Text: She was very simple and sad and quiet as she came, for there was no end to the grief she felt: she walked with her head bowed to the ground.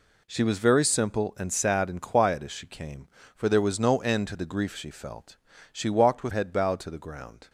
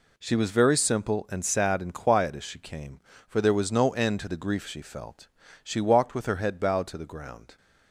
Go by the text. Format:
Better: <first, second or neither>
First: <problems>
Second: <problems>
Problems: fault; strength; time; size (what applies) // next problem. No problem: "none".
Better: second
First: skips "her"; at 6.3 s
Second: none